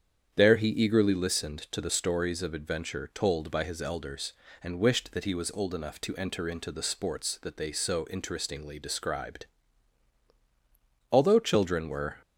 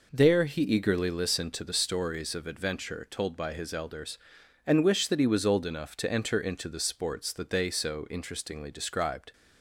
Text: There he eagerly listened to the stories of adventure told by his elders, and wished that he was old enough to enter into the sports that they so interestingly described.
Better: second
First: starts louder than the rest; strong; until 1.3 s; 8.5 dB // goes on to say "Although children were"; noticeable; from 11.1 s on; 1.1 s long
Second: none

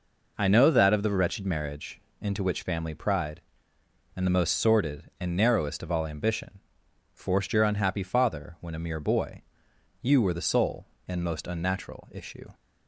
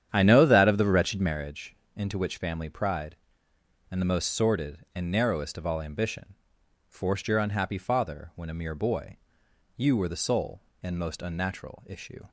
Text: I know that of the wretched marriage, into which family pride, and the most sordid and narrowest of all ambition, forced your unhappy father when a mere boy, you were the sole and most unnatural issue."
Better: first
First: none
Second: starts louder than the rest; strong; until 1.3 s; 9.5 dB

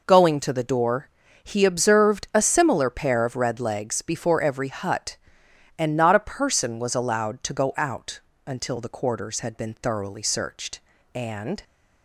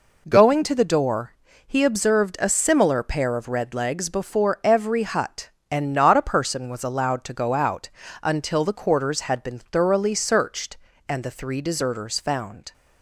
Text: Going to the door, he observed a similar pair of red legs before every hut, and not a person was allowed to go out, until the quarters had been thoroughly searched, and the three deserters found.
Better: second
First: stops before "the three deserters found"; at 11.6 s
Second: none

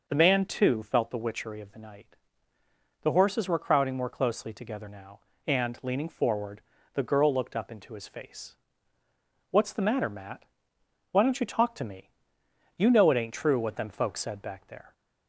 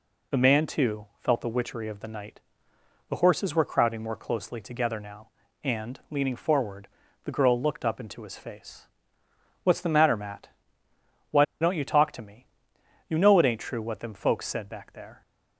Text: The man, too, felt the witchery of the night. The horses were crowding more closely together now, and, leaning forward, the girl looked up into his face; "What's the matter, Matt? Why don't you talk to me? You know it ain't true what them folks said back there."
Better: first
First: none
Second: pauses between "Why" and "don't"; slight; at 11.4 s; 0.17 s long

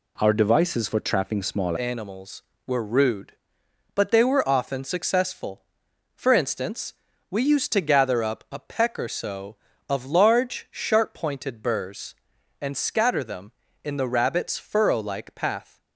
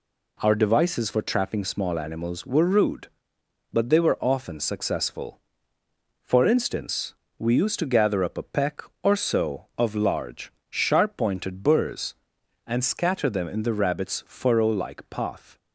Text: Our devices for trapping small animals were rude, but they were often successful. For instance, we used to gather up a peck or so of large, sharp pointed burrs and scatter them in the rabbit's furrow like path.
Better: second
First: changes voice at "animals"; from 1.7 s on; 14.0 s long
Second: none

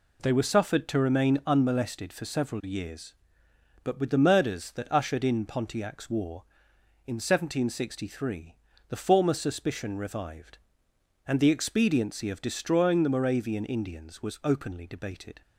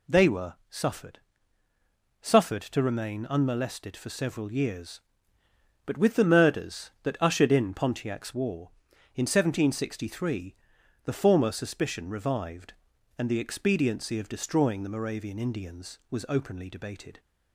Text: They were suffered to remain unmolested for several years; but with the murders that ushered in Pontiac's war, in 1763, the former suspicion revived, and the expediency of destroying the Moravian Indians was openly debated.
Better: first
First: none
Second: says "suffered" twice; at 2.2 s

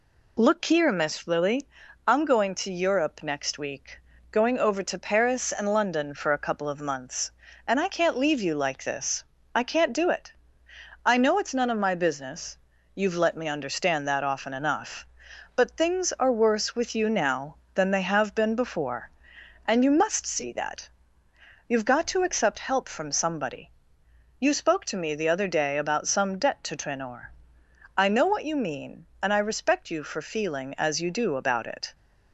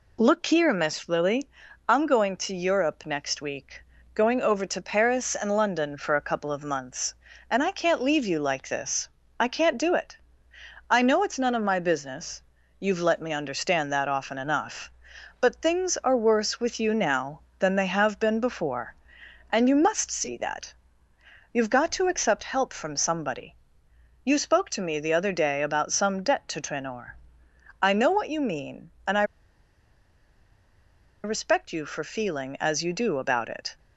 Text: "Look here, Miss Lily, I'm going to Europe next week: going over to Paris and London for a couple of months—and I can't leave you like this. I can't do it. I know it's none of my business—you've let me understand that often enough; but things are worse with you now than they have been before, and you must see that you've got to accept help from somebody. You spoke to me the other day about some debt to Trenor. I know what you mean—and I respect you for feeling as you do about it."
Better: first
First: pauses between "that" and "you've"; noticeable; at 20.8 s; 0.80 s long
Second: pauses between "that" and "you've"; noticeable; at 20.7 s; 0.80 s long // pauses between "I" and "respect"; strong; at 29.2 s; 2.0 s long

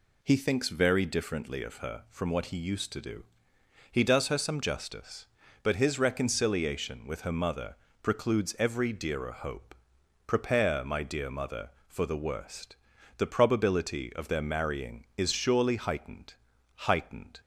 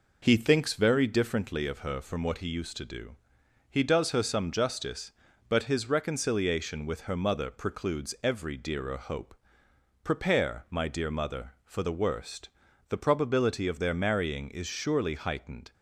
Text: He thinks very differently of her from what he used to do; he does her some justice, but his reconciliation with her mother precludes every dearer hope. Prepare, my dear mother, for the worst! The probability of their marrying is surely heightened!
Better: second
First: pauses between "mother" and "precludes"; slight; at 7.7 s; 0.28 s long // says "heightened" twice; at 16.8 s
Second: none

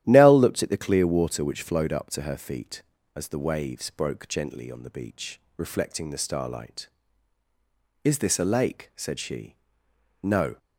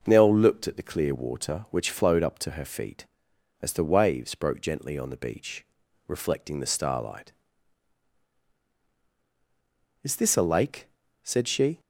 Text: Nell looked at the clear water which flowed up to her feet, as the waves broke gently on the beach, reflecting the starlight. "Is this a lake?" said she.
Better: second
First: starts louder than the rest; strong; until 1.0 s; 12 dB // goes on to say "No"; slight; from 10.2 s on; 0.36 s long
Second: none

